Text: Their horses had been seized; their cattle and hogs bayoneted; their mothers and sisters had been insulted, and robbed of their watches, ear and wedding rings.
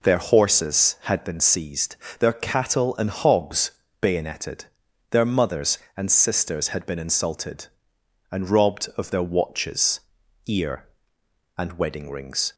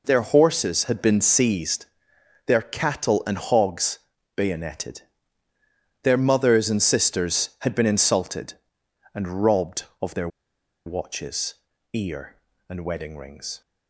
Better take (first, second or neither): first